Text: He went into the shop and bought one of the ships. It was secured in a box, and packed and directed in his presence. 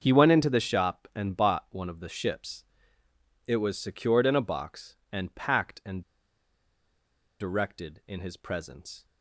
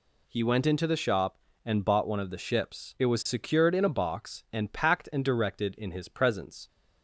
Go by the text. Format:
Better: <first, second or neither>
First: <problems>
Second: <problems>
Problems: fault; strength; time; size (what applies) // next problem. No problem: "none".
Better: second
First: starts louder than the rest; until 1.0 s; 6.5 dB // pauses between "and" and "directed"; strong; at 6.0 s; 1.3 s long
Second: none